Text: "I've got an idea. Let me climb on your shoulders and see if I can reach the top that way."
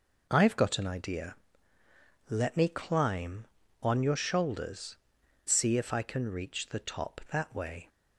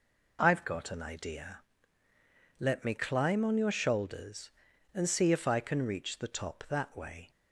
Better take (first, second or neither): second